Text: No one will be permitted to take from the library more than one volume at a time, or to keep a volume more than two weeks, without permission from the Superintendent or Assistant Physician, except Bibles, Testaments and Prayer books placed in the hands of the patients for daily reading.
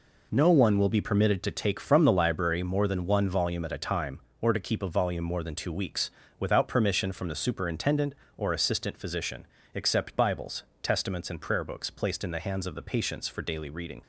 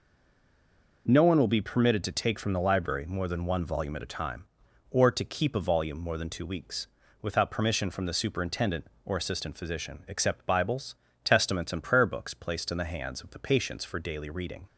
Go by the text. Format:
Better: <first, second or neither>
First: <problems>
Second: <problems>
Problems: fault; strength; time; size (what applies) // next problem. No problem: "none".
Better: first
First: none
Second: stays silent before the first word; until 1.0 s; 1.0 s long